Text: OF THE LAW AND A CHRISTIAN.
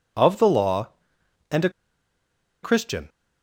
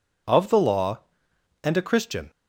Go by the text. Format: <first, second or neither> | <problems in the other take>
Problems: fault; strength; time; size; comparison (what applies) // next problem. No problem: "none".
second | pauses between "A" and "CHRISTIAN"; noticeable; at 1.6 s; 0.93 s long